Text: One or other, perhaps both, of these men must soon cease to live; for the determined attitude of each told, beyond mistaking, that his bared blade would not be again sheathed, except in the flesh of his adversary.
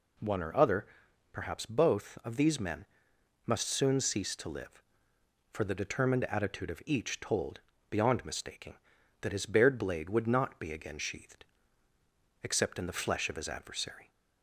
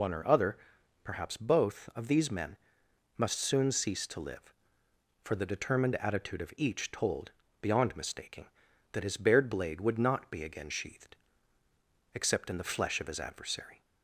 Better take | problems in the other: first | loses the start of "One"; at 0.0 s; 100 ms // pauses between "men" and "must"; noticeable; at 2.5 s; 0.60 s long; noticeable in the first

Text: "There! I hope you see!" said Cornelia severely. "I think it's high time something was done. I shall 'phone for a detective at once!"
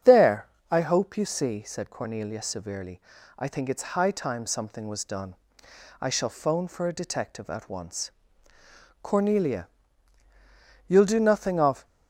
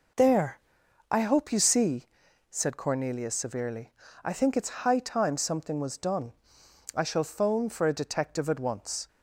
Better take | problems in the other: second | starts louder than the rest; strong; until 1.2 s; 8 dB // goes on to say "Cornelia you'll do nothing of"; strong; from 9.0 s on; 2.8 s long

